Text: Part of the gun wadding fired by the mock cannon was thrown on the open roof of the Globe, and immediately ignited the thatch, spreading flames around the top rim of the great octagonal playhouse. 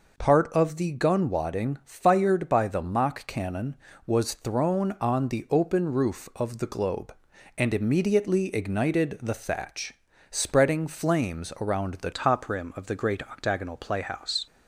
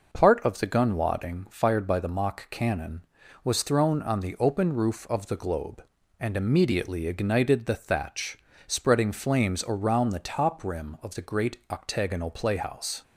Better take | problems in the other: second | changes voice at "top"; from 12.1 s on; 2.3 s long

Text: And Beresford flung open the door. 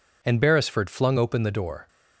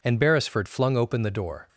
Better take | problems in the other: neither | none

